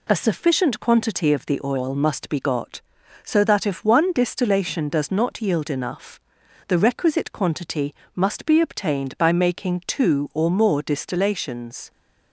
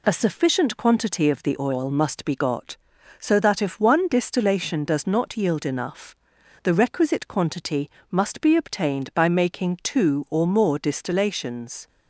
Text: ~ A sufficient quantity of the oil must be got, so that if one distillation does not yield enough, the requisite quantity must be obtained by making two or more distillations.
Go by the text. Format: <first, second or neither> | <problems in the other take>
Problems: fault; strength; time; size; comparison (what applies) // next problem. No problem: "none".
neither | pauses between "quantity" and "must"; slight; the same in both